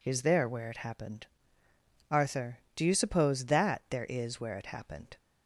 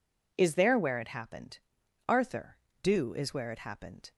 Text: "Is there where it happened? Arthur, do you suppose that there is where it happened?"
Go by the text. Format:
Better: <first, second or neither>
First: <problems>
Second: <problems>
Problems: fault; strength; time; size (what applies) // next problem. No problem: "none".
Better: first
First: none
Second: skips "you suppose that there"; at 3.1 s